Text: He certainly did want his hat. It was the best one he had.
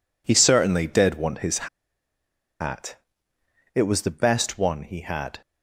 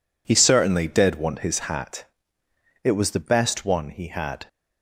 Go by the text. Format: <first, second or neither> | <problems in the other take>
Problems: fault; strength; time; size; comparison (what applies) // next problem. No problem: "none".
second | pauses between "his" and "hat"; noticeable; at 1.6 s; 0.92 s long